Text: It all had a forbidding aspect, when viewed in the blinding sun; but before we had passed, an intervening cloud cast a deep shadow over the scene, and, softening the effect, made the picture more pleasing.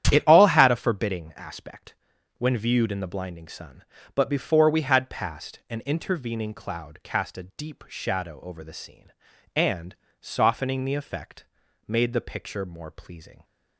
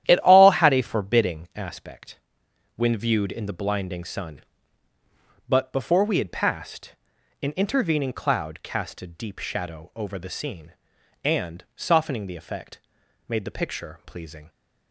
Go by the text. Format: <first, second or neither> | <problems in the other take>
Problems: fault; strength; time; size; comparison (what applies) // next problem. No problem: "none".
first | starts louder than the rest; strong; until 1.0 s; 11.5 dB; strong in the first // skips "more"; at 14.0 s